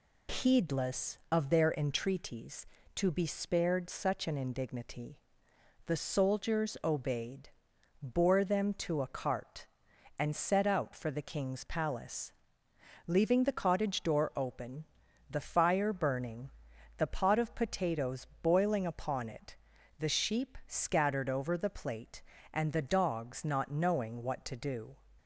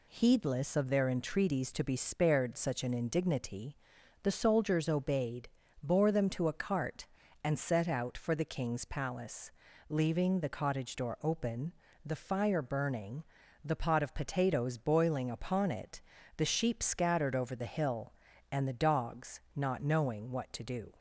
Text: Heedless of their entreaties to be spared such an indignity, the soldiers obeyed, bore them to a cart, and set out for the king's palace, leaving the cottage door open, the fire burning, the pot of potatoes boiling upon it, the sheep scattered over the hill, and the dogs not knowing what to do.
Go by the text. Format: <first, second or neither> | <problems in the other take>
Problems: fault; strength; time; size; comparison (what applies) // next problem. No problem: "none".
second | pauses between "potatoes" and "boiling"; slight; at 18.2 s; 0.16 s long // says "plate" for "hill"; at 21.6 s